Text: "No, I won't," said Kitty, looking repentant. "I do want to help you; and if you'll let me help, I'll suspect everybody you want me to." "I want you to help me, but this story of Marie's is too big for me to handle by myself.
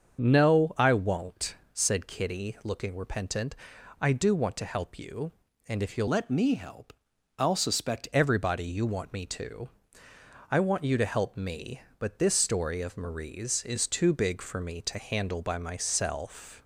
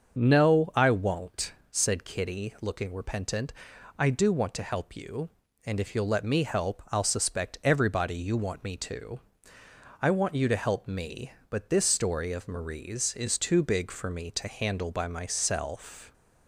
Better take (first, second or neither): second